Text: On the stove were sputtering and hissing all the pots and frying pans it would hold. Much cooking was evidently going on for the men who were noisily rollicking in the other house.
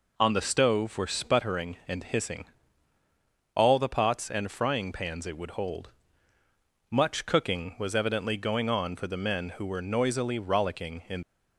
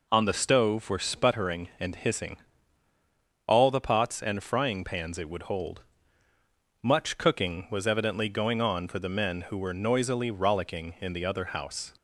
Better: second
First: pauses between "hissing" and "all"; at 2.4 s; 1.0 s long // stops before "the other house"; at 11.2 s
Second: pauses between "hissing" and "all"; at 2.3 s; 1.0 s long

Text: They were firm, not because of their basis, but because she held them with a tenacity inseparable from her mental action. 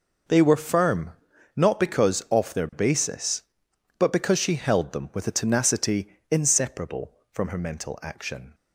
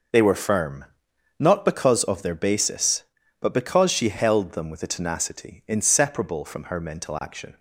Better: second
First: says "off" for "of"; at 2.2 s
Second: none

